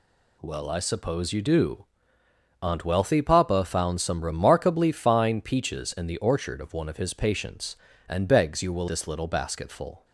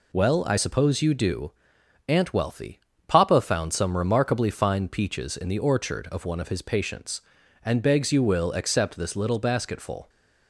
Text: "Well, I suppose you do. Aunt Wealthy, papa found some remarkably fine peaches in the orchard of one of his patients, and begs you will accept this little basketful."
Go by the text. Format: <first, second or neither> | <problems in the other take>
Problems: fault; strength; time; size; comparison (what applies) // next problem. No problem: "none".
second | skips "accept"; at 8.8 s